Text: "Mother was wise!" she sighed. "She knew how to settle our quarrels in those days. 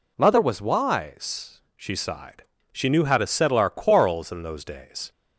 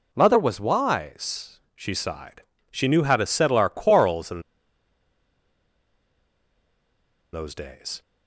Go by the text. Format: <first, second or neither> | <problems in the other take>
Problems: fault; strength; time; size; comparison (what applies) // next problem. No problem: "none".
first | pauses between "in" and "those"; strong; at 4.4 s; 2.9 s long